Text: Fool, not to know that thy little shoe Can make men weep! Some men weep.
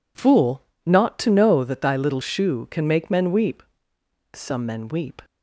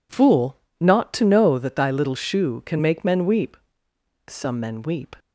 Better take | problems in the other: neither | none

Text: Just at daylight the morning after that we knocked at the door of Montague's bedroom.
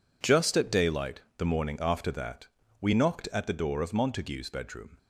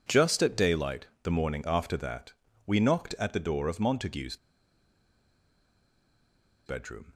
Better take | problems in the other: first | pauses between "daylight" and "the"; slight; at 1.0 s; 0.18 s long; slight in the first // pauses between "that" and "we"; slight; at 2.3 s; 0.34 s long; slight in the first // pauses between "Montague's" and "bedroom"; strong; at 4.3 s; 2.2 s long

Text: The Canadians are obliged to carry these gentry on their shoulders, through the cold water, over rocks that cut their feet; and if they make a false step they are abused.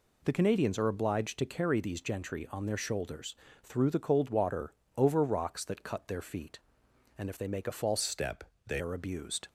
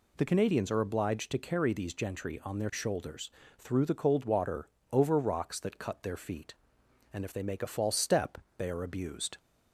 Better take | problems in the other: second | changes voice from "step" to "they"; from 8.0 to 8.8 s; 0.8 s long // pauses between "step" and "they"; slight; at 8.4 s; 0.24 s long; slight in the second

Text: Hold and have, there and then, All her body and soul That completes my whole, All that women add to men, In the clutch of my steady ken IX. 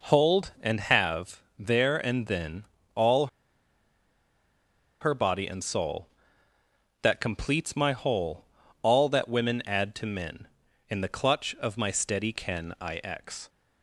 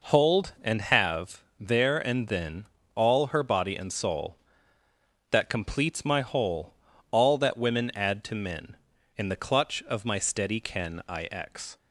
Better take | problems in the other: second | pauses between "All" and "her"; strong; at 3.2 s; 1.7 s long

